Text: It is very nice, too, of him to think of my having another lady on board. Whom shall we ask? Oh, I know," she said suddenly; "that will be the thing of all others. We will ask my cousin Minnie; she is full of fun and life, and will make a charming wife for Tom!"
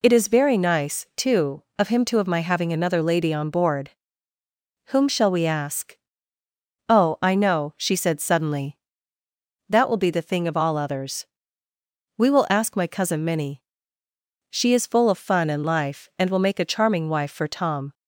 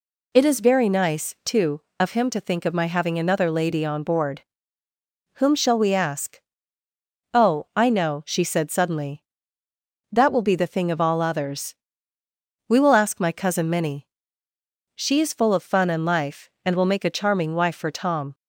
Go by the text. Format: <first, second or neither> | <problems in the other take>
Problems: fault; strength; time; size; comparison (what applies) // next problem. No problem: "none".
second | skips "think"; at 2.1 s